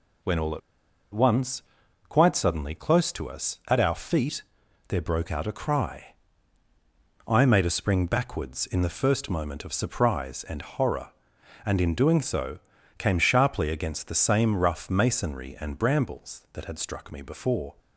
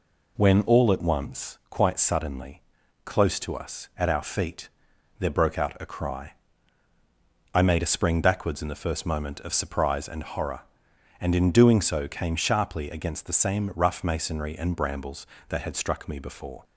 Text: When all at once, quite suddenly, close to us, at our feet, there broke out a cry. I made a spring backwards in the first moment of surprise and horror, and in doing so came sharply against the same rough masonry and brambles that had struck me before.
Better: second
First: pauses between "at" and "once"; noticeable; at 0.6 s; 0.53 s long // pauses between "so" and "came"; at 12.5 s; 0.40 s long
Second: none

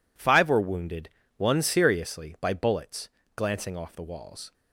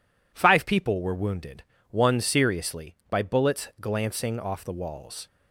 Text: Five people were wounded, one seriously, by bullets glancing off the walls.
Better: second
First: skips "people"; at 0.4 s // pauses between "bullets" and "glancing"; slight; at 3.0 s; 0.26 s long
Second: none

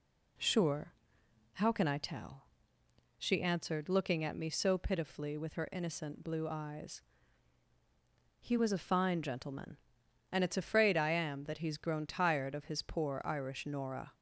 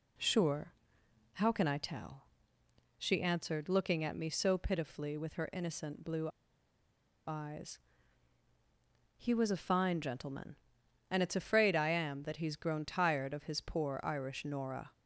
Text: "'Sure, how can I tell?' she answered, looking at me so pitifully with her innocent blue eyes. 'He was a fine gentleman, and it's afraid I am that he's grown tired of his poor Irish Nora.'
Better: first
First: none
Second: pauses between "blue" and "eyes"; at 6.2 s; 0.99 s long

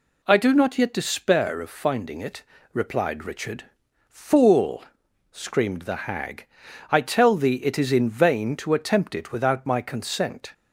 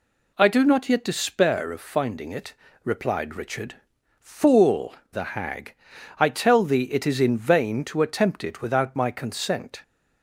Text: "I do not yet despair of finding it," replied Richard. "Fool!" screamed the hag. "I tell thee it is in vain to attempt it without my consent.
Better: first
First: none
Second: skips "screamed"; at 5.0 s

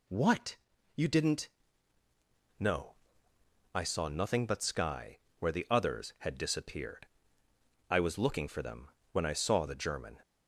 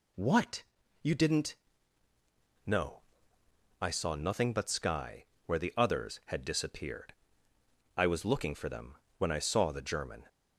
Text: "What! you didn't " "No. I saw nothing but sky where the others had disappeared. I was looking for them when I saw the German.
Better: neither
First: pauses between "sky" and "where"; slight; at 5.1 s; 0.22 s long // pauses between "them" and "when"; slight; at 8.9 s; 0.22 s long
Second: pauses between "sky" and "where"; slight; at 5.2 s; 0.22 s long // pauses between "them" and "when"; slight; at 8.9 s; 0.21 s long

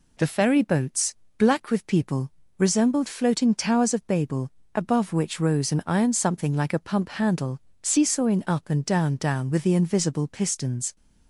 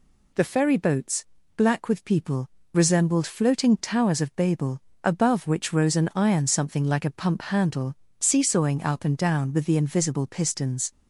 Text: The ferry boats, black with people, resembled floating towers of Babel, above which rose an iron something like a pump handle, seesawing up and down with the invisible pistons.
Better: second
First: says "down" twice; at 9.1 s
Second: none

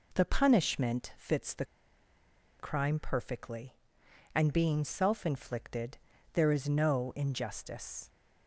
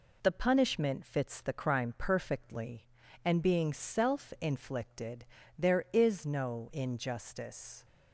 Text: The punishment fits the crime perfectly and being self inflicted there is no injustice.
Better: second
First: pauses between "the" and "crime"; noticeable; at 1.6 s; 0.94 s long // pauses between "inflicted" and "there"; slight; at 5.9 s; 0.34 s long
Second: pauses between "inflicted" and "there"; slight; at 5.2 s; 0.32 s long

